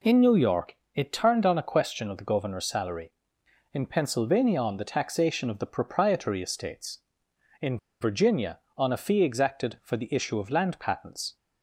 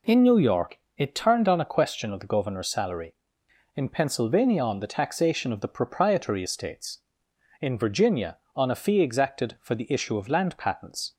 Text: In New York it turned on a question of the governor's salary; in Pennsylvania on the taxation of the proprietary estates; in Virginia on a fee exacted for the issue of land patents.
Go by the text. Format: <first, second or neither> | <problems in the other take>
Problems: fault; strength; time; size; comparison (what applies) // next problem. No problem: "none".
second | pauses between "York" and "it"; slight; at 0.7 s; 0.22 s long; slight in the second // pauses between "in" and "Virginia"; slight; at 7.7 s; 0.22 s long